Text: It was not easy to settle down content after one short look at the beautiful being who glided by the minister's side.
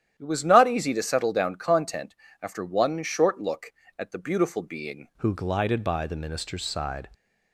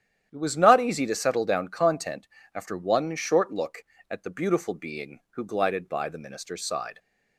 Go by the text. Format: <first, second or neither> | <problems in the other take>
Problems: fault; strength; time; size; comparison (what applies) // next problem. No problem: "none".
second | starts louder than the rest; strong; until 1.1 s; 10.5 dB; strong in the second // pauses between "content" and "after"; slight; at 2.1 s; 0.26 s long; slight in the second // changes voice at "who"; from 5.1 s on; 1.9 s long